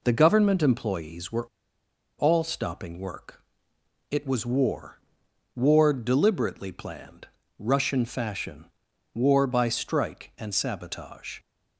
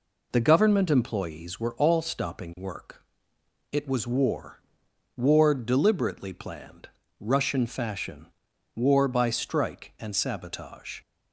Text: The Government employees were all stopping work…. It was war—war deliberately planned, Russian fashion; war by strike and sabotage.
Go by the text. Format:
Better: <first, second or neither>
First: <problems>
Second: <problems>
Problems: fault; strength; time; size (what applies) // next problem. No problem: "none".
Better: second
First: pauses between "were" and "all"; noticeable; at 1.4 s; 0.72 s long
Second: none